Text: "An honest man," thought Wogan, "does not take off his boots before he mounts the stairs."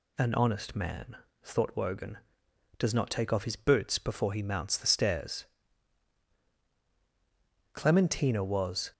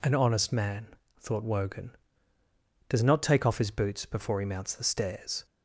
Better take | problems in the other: second | goes on to say "Clementina was"; noticeable; from 7.7 s on; 1.2 s long

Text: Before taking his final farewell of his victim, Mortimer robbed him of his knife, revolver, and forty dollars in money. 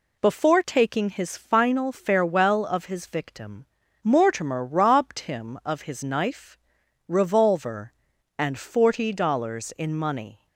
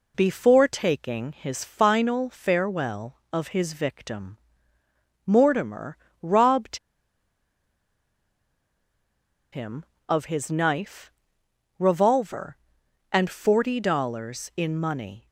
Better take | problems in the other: first | pauses between "Mortimer" and "robbed"; slight; at 5.9 s; 0.26 s long // pauses between "robbed" and "him"; strong; at 6.7 s; 2.7 s long

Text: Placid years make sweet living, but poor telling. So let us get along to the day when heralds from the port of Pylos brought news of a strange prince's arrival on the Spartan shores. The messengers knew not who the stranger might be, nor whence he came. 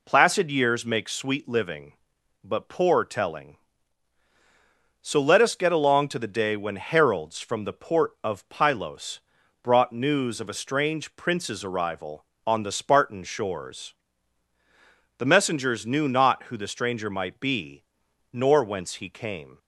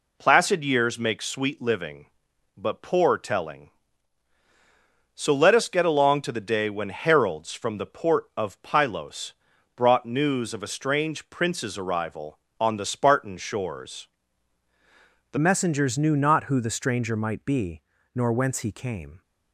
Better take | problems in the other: first | pauses between "Pylos" and "brought"; at 9.3 s; 0.42 s long; also in the first // changes voice at "messengers"; from 15.3 s on; 3.9 s long

